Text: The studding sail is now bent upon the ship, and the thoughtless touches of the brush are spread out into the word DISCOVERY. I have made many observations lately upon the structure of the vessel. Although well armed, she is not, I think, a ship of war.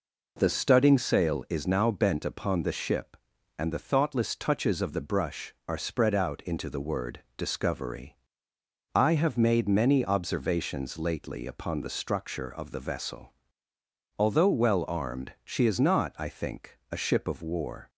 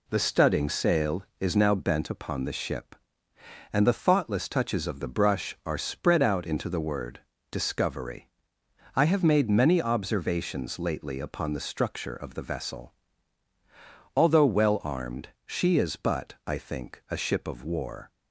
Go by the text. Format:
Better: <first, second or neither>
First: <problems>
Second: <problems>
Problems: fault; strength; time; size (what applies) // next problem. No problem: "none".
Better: first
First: pauses between "word" and "DISCOVERY"; slight; at 7.2 s; 0.16 s long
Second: pauses between "word" and "DISCOVERY"; slight; at 7.1 s; 0.32 s long // says "but" for "not"; at 15.9 s